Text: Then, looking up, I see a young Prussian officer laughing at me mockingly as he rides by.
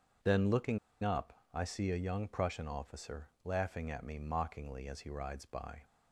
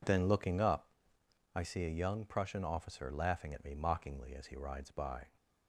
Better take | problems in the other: second | starts louder than the rest; until 1.7 s; 7 dB // pauses between "looking" and "up"; slight; at 0.7 s; 0.25 s long

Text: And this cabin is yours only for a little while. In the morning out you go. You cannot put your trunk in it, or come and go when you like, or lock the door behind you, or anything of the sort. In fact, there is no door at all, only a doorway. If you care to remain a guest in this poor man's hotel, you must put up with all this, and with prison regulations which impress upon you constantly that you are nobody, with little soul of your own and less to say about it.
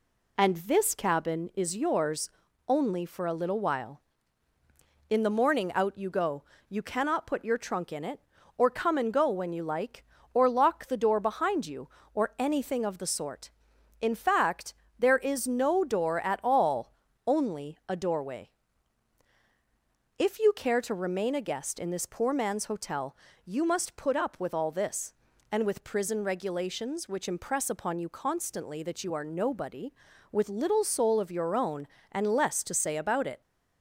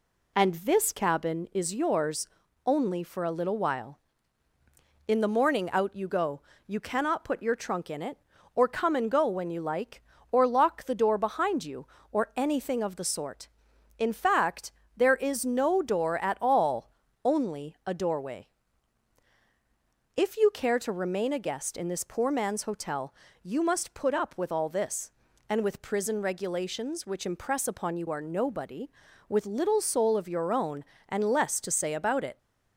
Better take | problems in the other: first | pauses between "yours" and "only"; at 2.2 s; 0.38 s long; also in the first // skips "constantly that you"; at 28.0 s

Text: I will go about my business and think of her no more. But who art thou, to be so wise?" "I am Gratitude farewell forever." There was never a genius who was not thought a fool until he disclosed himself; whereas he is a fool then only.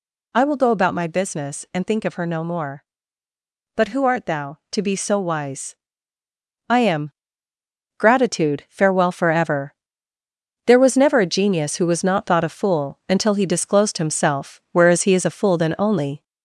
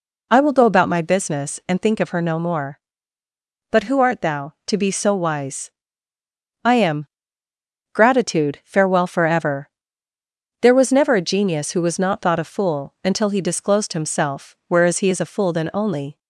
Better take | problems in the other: second | gets louder; slight; throughout; 2.5 dB // pauses between "am" and "Gratitude"; noticeable; at 7.1 s; 0.86 s long; noticeable in the second

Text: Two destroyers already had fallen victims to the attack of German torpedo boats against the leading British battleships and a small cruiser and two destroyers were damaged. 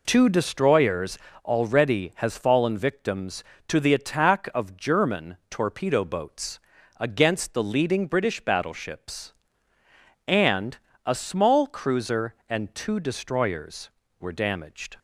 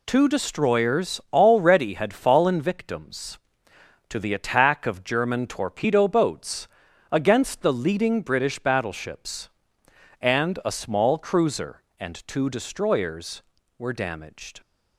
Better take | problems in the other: second | pauses between "destroyers" and "already"; slight; at 1.1 s; 0.26 s long // says "has" for "had"; at 2.1 s // pauses between "boats" and "against"; at 6.6 s; 0.38 s long; also in the second // pauses between "and" and "a"; slight; at 10.7 s; 0.26 s long

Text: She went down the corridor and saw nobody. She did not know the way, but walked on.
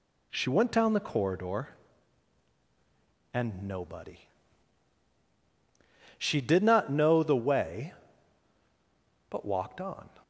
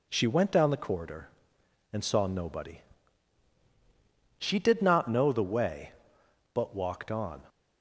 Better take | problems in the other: second | skips "saw"; at 3.6 s

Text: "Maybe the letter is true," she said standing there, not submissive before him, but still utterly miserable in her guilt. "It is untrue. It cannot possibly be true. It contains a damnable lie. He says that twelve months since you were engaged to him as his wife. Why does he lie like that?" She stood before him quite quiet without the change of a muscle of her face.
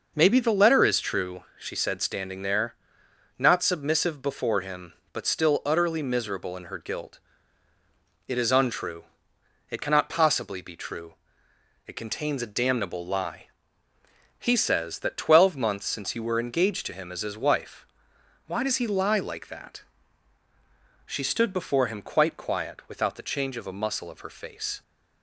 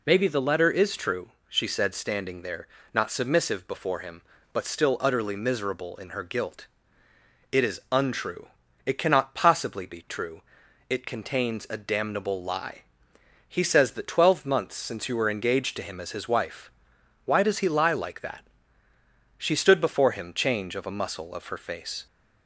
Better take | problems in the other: first | skips "quite quiet without the"; at 20.3 s

